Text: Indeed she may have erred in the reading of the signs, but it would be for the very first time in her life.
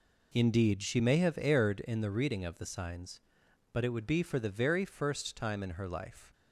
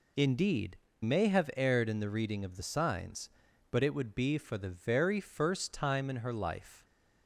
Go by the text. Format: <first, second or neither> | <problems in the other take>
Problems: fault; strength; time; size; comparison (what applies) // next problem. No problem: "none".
first | skips "she"; at 0.8 s